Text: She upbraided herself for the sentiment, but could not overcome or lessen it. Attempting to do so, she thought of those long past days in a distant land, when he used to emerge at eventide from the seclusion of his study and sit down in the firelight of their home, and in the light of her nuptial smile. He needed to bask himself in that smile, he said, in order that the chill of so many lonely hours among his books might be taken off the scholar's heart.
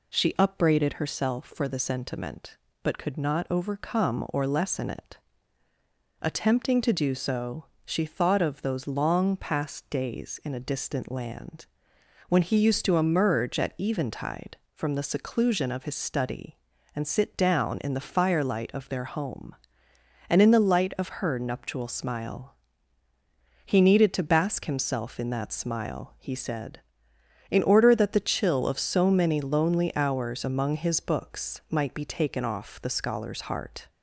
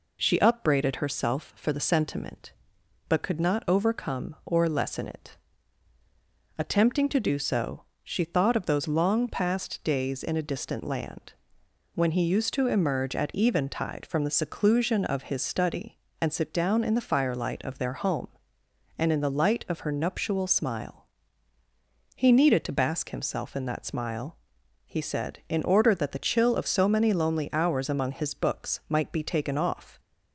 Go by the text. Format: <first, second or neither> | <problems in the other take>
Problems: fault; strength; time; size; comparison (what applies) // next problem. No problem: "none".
first | stops before "the scholar's heart"; at 29.9 s